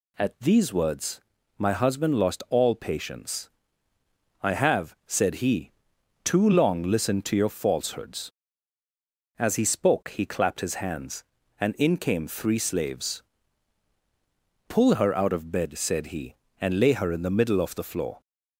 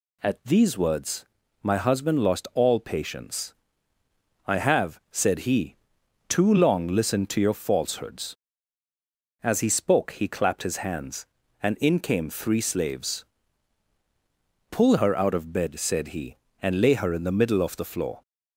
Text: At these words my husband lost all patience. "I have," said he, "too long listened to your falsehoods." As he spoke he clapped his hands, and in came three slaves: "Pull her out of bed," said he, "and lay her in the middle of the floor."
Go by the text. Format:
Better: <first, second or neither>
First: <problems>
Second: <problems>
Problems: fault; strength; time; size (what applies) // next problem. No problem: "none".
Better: neither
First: pauses between "words" and "my"; at 1.2 s; 0.38 s long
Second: pauses between "words" and "my"; at 1.2 s; 0.38 s long